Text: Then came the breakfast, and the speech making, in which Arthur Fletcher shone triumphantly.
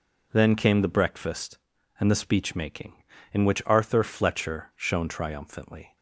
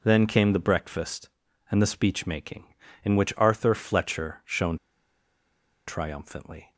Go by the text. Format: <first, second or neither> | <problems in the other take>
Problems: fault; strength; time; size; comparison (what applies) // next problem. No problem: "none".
first | pauses between "shone" and "triumphantly"; at 4.7 s; 1.1 s long